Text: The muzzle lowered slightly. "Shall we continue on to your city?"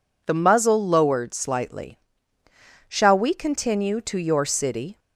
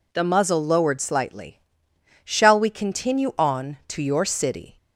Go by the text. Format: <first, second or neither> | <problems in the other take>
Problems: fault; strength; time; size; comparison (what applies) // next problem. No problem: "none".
second | skips "on"; at 3.9 s